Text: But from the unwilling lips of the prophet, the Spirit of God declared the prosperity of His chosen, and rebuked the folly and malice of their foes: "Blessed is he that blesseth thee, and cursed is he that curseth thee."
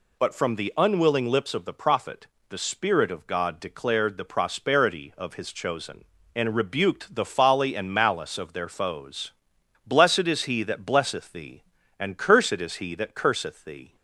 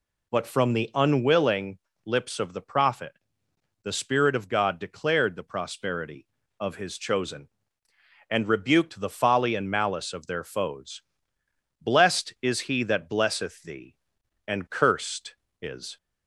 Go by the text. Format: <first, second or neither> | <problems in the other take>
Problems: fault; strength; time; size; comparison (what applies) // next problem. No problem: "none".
first | pauses between "unwilling" and "lips"; slight; at 1.7 s; 0.26 s long // stops before "he that curseth thee"; at 15.9 s